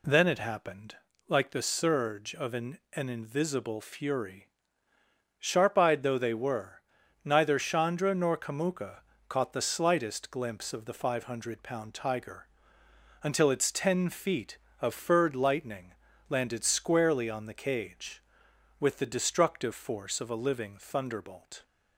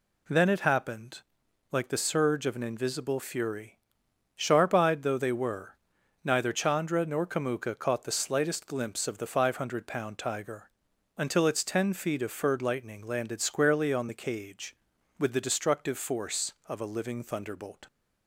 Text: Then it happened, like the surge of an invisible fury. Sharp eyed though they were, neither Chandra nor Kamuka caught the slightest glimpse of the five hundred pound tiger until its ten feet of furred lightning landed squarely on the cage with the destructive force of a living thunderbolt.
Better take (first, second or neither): second